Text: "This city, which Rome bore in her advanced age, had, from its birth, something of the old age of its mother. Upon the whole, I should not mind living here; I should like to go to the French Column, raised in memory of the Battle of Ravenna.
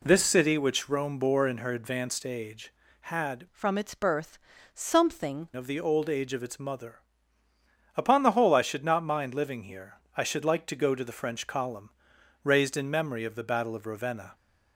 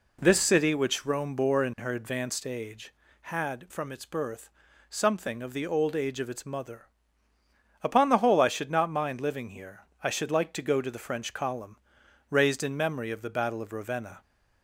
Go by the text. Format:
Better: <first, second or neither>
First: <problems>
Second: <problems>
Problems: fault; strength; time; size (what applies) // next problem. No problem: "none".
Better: second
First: changes voice from "from" to "something"; from 3.5 to 5.4 s; 1.9 s long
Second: none